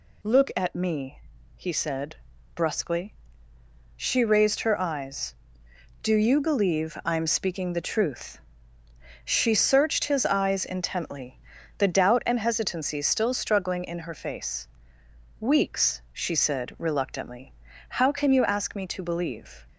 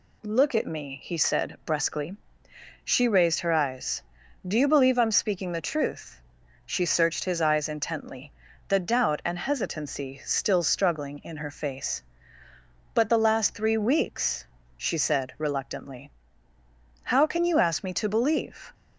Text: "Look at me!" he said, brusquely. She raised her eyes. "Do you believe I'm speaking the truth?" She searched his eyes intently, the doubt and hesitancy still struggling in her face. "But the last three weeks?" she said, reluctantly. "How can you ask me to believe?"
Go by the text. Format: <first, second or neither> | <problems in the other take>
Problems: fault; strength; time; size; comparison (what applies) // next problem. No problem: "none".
second | skips "But the last three"; at 15.0 s